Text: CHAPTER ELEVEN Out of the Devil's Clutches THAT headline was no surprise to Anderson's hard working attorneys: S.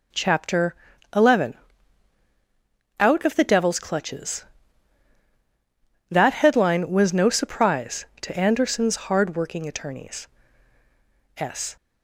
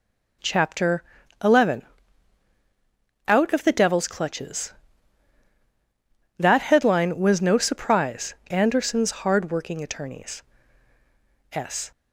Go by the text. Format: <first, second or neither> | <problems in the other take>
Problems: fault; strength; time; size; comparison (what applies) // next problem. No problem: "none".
first | pauses between "CHAPTER" and "ELEVEN"; at 1.0 s; 0.38 s long; also in the first // pauses between "ELEVEN" and "Out"; strong; at 1.8 s; 1.4 s long; strong in the first // skips "to"; at 8.4 s